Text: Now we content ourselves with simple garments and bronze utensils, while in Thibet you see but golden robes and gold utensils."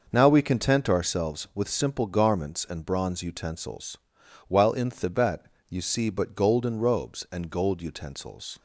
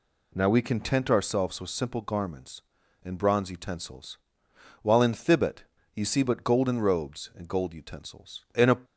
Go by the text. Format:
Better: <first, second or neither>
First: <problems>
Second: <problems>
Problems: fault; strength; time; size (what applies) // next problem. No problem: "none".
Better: first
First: pauses between "Thibet" and "you"; slight; at 5.4 s; 0.24 s long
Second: pauses between "Thibet" and "you"; slight; at 5.6 s; 0.32 s long // goes on to say "In a"; slight; from 8.5 s on; 0.22 s long